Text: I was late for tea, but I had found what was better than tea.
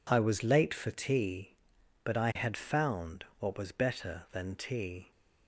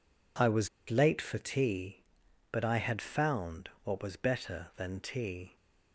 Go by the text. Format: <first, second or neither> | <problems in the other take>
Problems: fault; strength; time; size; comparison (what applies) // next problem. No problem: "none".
first | pauses between "was" and "late"; slight; at 0.6 s; 0.20 s long // pauses between "found" and "what"; slight; at 3.6 s; 0.16 s long; slight in the first